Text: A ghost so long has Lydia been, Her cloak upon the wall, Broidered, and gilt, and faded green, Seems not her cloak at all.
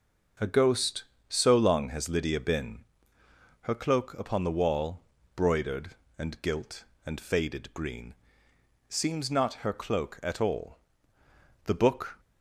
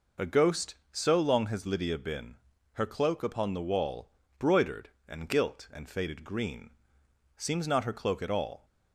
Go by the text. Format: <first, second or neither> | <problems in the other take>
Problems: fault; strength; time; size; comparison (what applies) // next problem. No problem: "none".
second | starts louder than the rest; until 1.6 s; 6.5 dB // goes on to say "The book"; from 11.6 s on; 0.56 s long